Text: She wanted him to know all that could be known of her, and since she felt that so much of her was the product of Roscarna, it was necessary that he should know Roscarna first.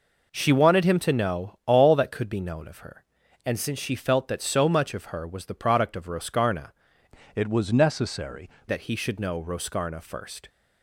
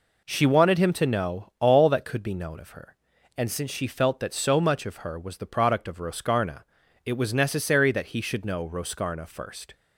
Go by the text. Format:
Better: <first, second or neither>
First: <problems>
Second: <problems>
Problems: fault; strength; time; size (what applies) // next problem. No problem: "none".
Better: second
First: changes voice from "it" to "necessary"; from 7.3 to 8.5 s; 1.2 s long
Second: none